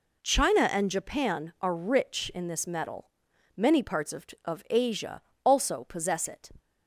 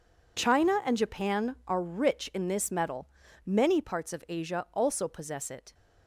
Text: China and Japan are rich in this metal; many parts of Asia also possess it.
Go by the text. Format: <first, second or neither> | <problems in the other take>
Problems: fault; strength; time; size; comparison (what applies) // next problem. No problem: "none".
second | says "of" twice; at 4.4 s // pauses between "Asia" and "also"; slight; at 5.2 s; 0.22 s long